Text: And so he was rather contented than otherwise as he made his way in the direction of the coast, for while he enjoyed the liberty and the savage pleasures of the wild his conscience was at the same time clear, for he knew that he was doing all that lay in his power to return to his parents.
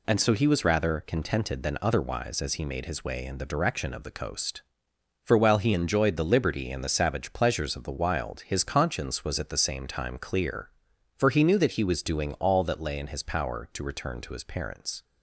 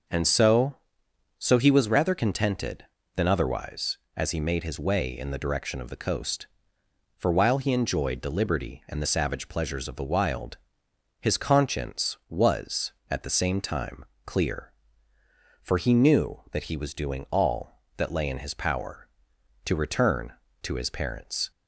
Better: first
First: none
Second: starts louder than the rest; noticeable; until 1.7 s; 6 dB // says "so" twice; at 1.3 s // pauses between "wild" and "his"; noticeable; at 10.5 s; 0.64 s long // pauses between "time" and "clear"; slight; at 14.0 s; 0.22 s long

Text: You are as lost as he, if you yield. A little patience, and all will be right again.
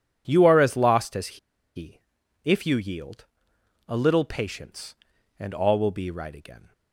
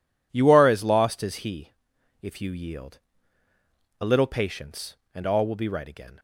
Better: second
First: pauses between "as" and "he"; at 1.3 s; 0.37 s long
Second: none

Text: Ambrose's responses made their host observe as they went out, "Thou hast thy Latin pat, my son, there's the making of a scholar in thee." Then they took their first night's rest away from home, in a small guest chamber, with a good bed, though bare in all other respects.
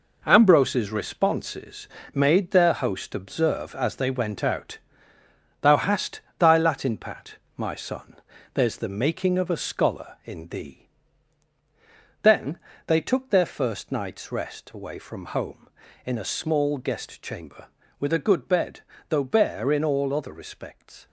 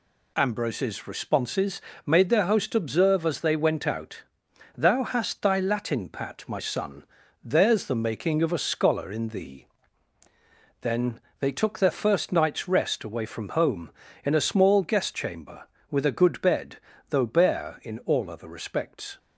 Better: second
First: gets quieter; strong; throughout; 8 dB // pauses between "responses" and "made"; slight; at 1.8 s; 0.26 s long // pauses between "hast" and "thy"; slight; at 6.2 s; 0.18 s long // pauses between "Then" and "they"; slight; at 12.5 s; 0.26 s long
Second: pauses between "responses" and "made"; slight; at 1.8 s; 0.24 s long // pauses between "Then" and "they"; slight; at 11.2 s; 0.18 s long

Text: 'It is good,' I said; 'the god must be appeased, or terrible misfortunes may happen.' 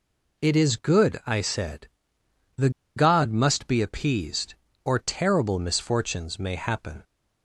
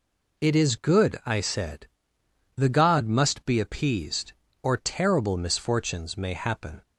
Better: second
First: pauses between "the" and "god"; slight; at 2.6 s; 0.26 s long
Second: none

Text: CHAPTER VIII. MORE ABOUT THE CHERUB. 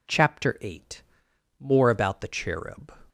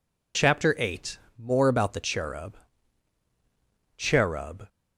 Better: first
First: none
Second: says "CHERUB" twice; at 3.9 s

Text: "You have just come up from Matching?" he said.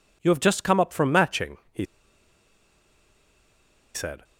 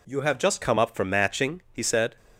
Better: second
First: pauses between "he" and "said"; strong; at 1.8 s; 2.0 s long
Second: none

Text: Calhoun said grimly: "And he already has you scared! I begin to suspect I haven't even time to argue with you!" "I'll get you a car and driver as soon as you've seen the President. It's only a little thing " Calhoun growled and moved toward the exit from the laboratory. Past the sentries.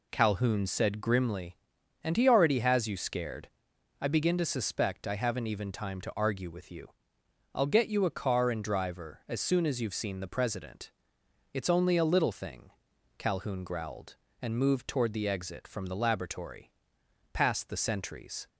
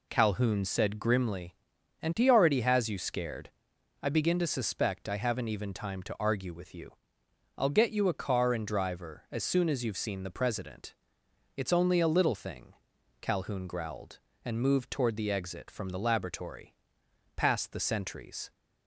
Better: neither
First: none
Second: none

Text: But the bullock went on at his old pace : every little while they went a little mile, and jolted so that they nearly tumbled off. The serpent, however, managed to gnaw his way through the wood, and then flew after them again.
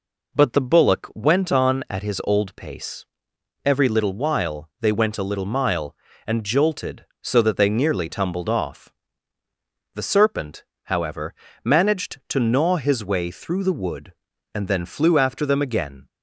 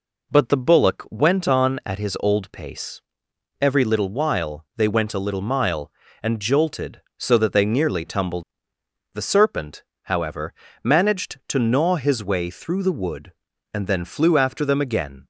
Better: first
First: none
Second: skips "off"; at 8.7 s

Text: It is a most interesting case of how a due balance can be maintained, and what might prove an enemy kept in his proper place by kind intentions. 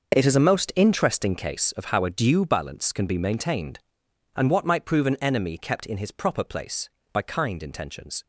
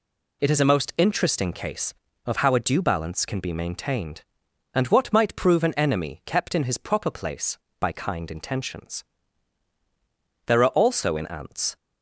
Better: first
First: none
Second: goes on to say "There are also in ants"; noticeable; from 10.4 s on; 1.3 s long

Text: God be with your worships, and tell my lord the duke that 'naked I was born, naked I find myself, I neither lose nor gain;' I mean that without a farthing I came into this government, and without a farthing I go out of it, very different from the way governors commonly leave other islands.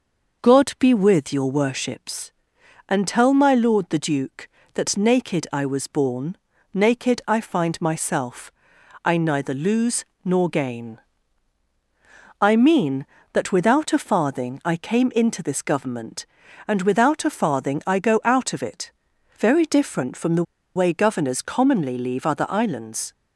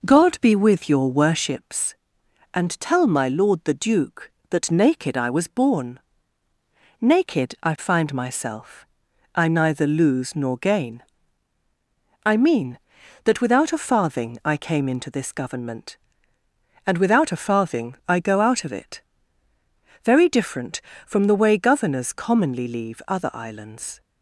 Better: second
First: pauses between "lose" and "nor"; slight; at 10.0 s; 0.18 s long // pauses between "the" and "way"; slight; at 20.4 s; 0.30 s long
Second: none

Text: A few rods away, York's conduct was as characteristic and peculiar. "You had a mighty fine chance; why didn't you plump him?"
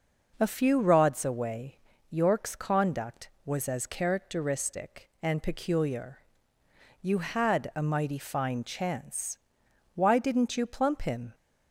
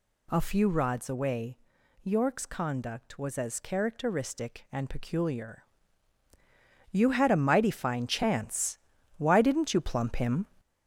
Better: first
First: none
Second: gets louder; noticeable; throughout; 5.5 dB

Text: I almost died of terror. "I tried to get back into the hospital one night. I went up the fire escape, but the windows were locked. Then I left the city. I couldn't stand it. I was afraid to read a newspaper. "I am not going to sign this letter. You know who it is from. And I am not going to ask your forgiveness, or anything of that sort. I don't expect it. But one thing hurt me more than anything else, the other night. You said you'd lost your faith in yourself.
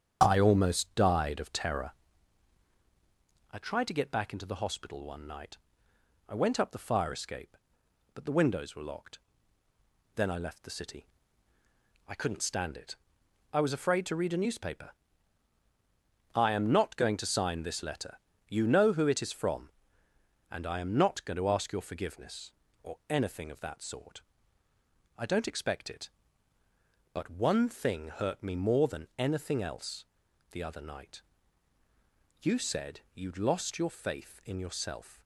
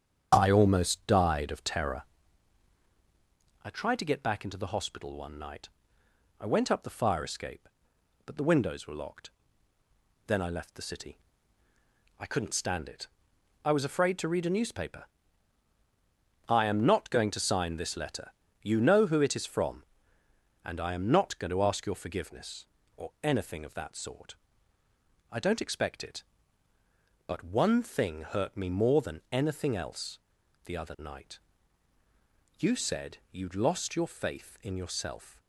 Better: neither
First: starts louder than the rest; strong; until 1.2 s; 8.5 dB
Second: starts louder than the rest; strong; until 1.3 s; 8 dB

